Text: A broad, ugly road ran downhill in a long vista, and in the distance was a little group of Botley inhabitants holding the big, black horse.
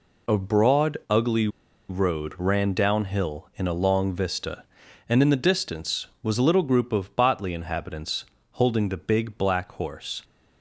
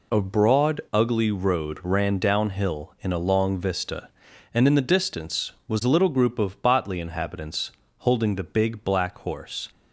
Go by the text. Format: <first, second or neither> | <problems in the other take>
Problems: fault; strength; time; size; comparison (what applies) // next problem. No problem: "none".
second | pauses between "ugly" and "road"; at 1.4 s; 0.40 s long // pauses between "inhabitants" and "holding"; slight; at 8.2 s; 0.26 s long; slight in the second